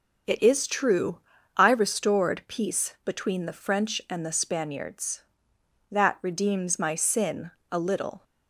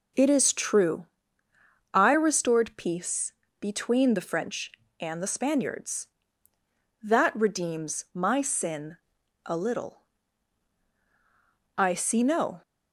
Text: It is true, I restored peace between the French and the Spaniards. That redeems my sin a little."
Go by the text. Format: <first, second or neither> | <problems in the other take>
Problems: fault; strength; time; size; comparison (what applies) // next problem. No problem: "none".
first | pauses between "peace" and "between"; slight; at 3.3 s; 0.28 s long // pauses between "sin" and "a"; noticeable; at 8.9 s; 0.48 s long; slight in the first // goes on to say "I see no"; noticeable; from 11.7 s on; 0.86 s long